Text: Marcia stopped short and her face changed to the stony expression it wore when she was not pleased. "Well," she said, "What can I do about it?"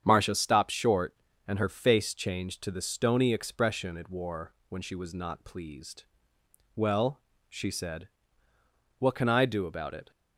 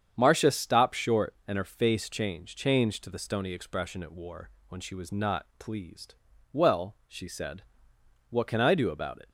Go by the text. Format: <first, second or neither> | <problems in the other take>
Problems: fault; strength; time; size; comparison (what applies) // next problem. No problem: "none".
first | starts louder than the rest; strong; until 1.1 s; 8 dB; strong in the first // says "changed" twice; at 2.5 s // pauses between "wore" and "when"; slight; at 4.4 s; 0.20 s long